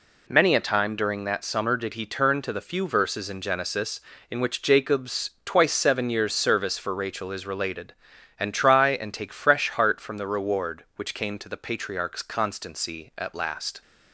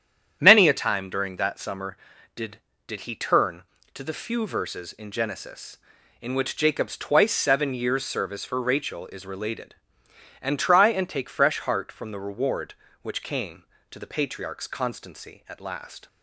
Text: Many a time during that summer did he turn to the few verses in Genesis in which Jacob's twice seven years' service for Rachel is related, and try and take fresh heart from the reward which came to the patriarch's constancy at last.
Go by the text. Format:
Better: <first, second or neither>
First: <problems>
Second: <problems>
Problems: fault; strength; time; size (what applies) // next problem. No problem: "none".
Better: first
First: none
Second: starts louder than the rest; strong; until 1.4 s; 9 dB // says "did" twice; at 2.8 s